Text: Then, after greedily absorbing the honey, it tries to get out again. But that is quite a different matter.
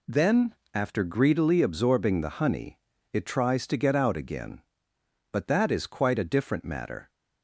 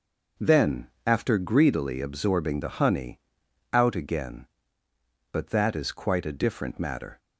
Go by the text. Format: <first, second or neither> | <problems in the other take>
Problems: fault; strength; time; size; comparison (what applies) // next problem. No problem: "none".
first | skips "it tries to get"; at 3.4 s